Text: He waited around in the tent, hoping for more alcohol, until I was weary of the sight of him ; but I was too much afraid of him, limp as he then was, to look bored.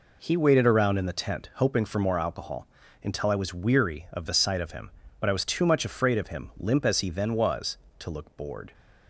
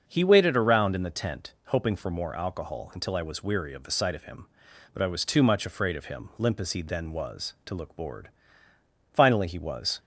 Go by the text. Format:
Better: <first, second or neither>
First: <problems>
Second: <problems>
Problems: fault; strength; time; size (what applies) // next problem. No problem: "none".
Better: first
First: none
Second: starts louder than the rest; until 1.0 s; 6.5 dB // goes on to say "Finally he was"; noticeable; from 9.1 s on; 0.88 s long